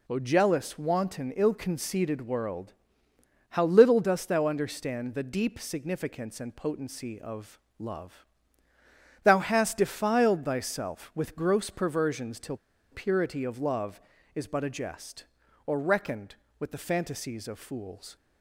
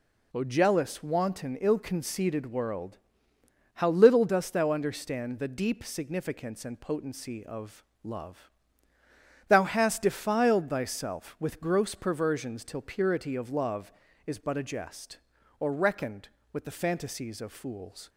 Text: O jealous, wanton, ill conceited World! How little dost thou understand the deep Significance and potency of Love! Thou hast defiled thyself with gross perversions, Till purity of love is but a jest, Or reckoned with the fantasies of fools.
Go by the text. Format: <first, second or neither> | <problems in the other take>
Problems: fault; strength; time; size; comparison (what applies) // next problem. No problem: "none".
second | pauses between "of" and "Love"; slight; at 7.5 s; 0.22 s long; slight in the second // pauses between "Till" and "purity"; slight; at 12.5 s; 0.35 s long